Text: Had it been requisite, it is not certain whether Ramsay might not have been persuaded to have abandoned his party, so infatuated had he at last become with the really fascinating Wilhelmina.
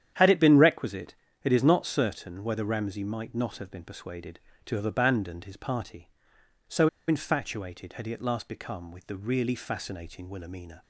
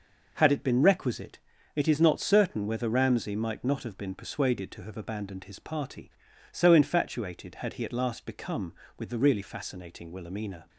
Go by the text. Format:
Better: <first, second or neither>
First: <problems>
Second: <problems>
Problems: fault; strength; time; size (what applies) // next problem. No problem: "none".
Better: second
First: starts louder than the rest; strong; until 1.4 s; 9.5 dB // pauses between "so" and "infatuated"; slight; at 6.8 s; 0.20 s long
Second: none